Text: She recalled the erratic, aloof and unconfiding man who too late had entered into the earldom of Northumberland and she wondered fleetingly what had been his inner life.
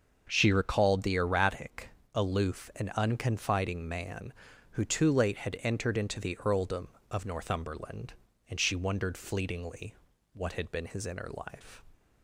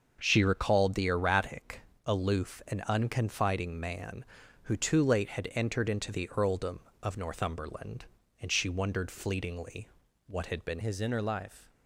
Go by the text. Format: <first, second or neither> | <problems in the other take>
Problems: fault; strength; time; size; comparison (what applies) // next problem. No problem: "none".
first | starts louder than the rest; until 1.2 s; 6.5 dB; also in the first // pauses between "fleetingly" and "what"; at 9.8 s; 0.40 s long; also in the first // changes voice at "his"; from 10.8 s on; 0.9 s long